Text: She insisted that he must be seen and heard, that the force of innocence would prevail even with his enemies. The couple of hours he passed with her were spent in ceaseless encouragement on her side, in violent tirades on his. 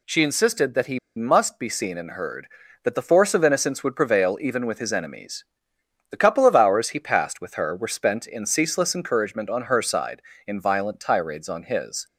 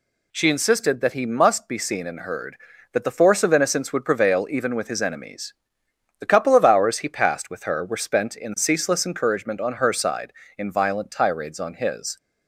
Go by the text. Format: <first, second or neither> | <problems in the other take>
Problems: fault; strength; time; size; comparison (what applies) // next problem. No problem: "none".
second | pauses between "he" and "must"; slight; at 0.9 s; 0.17 s long